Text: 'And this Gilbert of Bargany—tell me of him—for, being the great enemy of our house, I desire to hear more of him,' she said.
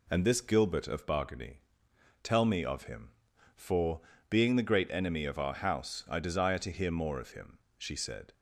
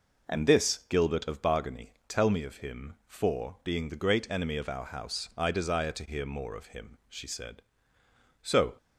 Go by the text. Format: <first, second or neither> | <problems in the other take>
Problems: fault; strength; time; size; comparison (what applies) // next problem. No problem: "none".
first | goes on to say "So"; slight; from 8.4 s on; 0.32 s long